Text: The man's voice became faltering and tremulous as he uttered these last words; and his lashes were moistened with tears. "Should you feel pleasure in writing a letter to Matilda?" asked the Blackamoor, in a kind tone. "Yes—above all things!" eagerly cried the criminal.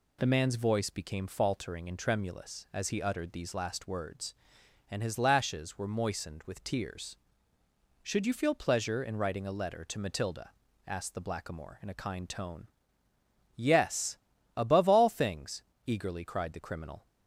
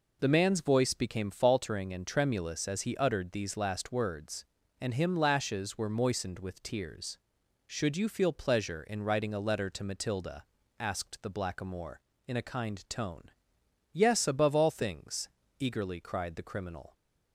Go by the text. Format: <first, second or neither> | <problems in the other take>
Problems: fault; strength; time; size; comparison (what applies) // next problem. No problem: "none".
first | says "him" for "his"; at 4.9 s